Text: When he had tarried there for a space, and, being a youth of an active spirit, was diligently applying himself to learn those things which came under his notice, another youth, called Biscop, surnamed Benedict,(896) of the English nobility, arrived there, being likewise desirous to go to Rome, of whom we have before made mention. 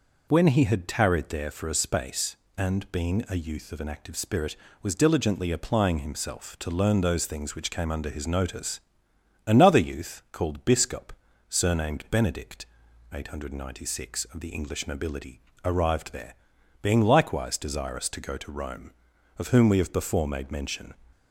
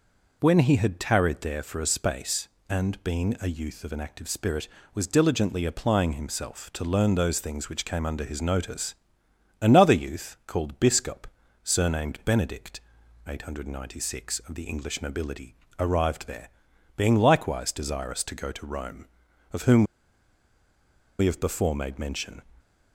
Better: first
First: none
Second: pauses between "whom" and "we"; strong; at 19.8 s; 1.3 s long

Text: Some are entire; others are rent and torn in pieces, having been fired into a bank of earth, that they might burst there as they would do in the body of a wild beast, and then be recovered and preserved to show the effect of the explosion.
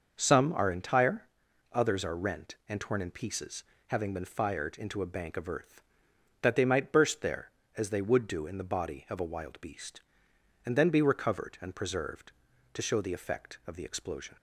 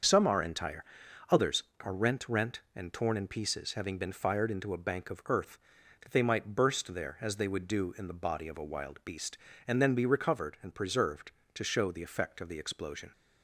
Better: first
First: starts louder than the rest; until 1.1 s; 6 dB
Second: starts louder than the rest; until 1.5 s; 6.5 dB // says "rent" twice; at 2.2 s

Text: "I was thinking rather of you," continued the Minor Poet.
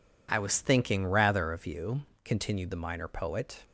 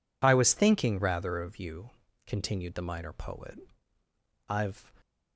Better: first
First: none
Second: goes on to say "I've"; slight; from 4.4 s on; 0.46 s long

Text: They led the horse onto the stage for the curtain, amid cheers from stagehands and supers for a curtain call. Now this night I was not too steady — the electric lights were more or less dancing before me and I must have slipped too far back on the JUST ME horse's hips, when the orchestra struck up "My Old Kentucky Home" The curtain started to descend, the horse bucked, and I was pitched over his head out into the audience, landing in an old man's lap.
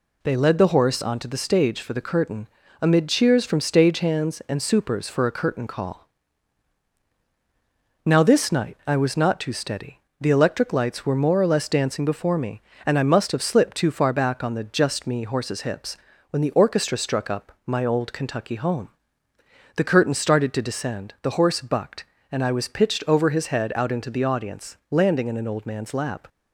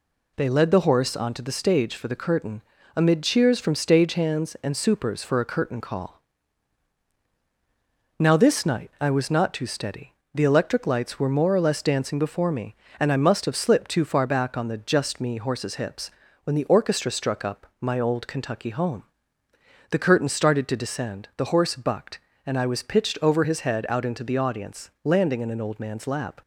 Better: neither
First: pauses between "Home" and "The"; noticeable; at 18.8 s; 0.88 s long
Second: pauses between "Home" and "The"; noticeable; at 19.0 s; 0.88 s long

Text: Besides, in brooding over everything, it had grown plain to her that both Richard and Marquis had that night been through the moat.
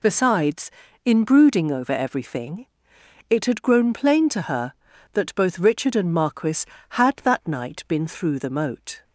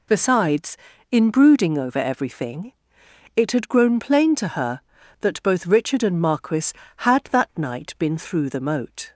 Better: neither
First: none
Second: none

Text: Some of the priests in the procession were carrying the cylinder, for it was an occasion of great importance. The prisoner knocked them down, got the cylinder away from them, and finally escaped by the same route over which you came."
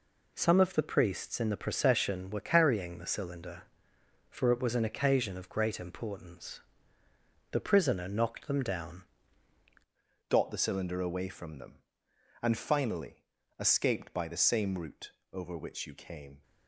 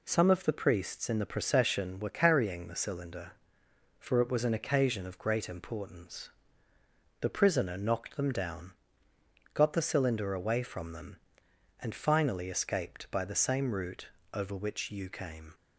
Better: second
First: changes voice at "got"; from 10.2 s on; 6.2 s long // pauses between "finally" and "escaped"; slight; at 13.2 s; 0.34 s long // pauses between "route" and "over"; slight; at 15.1 s; 0.22 s long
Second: pauses between "route" and "over"; slight; at 14.0 s; 0.26 s long

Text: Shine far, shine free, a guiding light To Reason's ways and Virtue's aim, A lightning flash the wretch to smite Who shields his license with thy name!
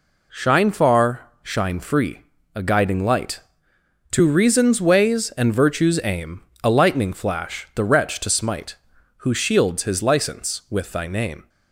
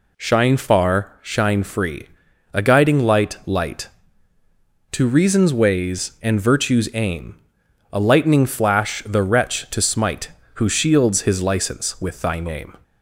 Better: first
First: none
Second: says "light" twice; at 3.4 s

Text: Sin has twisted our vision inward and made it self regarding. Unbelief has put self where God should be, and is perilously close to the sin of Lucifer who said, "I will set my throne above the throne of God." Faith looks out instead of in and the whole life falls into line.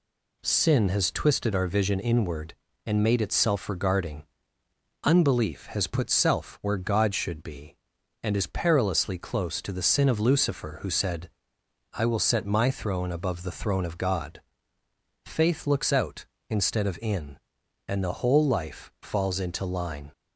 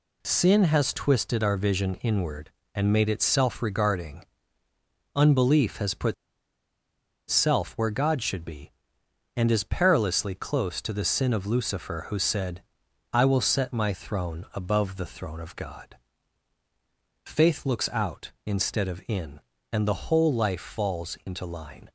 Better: first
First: none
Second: pauses between "put" and "self"; at 6.1 s; 1.1 s long

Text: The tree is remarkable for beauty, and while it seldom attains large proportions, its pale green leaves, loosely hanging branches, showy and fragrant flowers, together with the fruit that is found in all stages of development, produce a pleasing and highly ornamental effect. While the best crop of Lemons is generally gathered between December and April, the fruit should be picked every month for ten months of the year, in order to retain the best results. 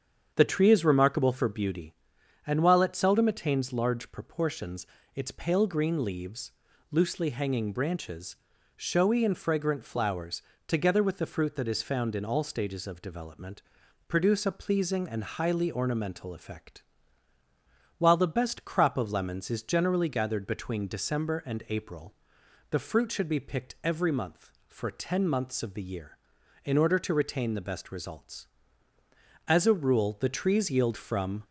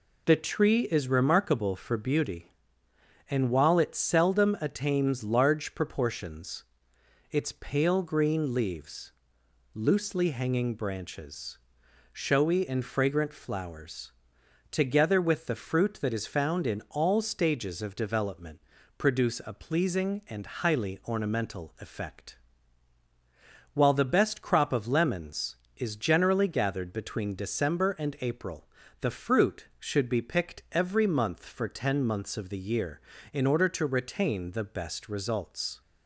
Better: second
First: starts louder than the rest; strong; until 1.3 s; 8 dB // goes on to say "As a rule the trees yield from"; strong; from 29.4 s on; 1.9 s long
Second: none

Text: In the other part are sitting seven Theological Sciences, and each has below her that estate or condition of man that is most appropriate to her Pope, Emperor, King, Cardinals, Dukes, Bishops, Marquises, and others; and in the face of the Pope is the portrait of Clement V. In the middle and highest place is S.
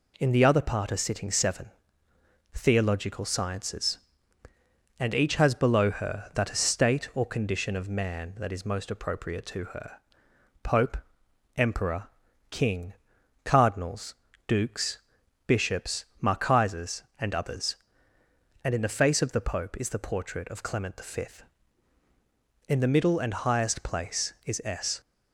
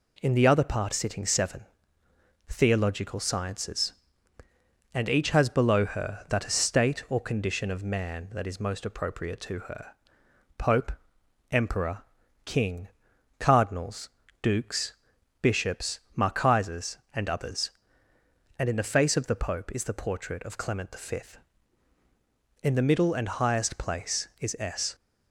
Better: first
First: pauses between "seven" and "Theological"; noticeable; at 1.7 s; 0.84 s long // pauses between "her" and "Pope"; noticeable; at 9.9 s; 0.66 s long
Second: skips "are"; at 0.9 s // pauses between "seven" and "Theological"; noticeable; at 1.6 s; 0.84 s long // pauses between "her" and "Pope"; noticeable; at 9.9 s; 0.66 s long

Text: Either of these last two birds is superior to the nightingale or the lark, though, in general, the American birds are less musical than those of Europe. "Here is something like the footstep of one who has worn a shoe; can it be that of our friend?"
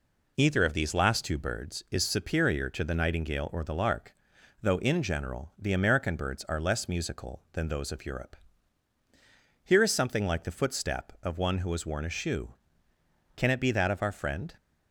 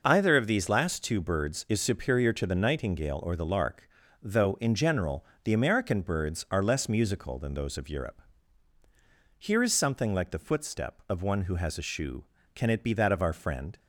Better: first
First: none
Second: skips "worn"; at 11.7 s

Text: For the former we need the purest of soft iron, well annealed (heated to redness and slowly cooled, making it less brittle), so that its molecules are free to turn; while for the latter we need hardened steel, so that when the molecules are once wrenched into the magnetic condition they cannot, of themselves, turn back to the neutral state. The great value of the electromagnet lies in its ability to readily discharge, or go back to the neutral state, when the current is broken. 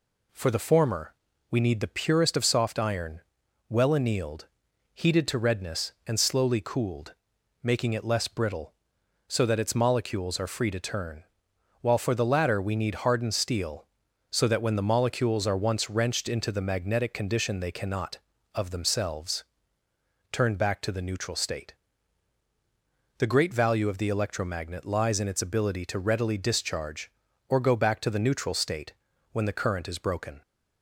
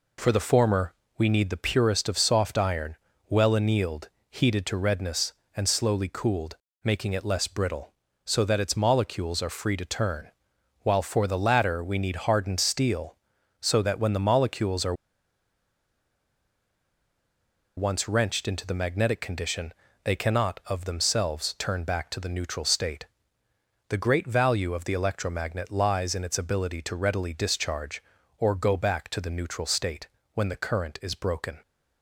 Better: first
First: pauses between "former" and "we"; slight; at 1.1 s; 0.36 s long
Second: pauses between "former" and "we"; slight; at 0.9 s; 0.26 s long // pauses between "are" and "once"; strong; at 14.9 s; 2.8 s long // pauses between "condition" and "they"; slight; at 19.7 s; 0.32 s long

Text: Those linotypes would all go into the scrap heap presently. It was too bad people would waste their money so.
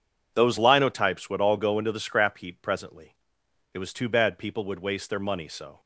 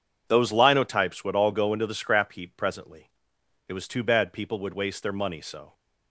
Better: neither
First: none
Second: none

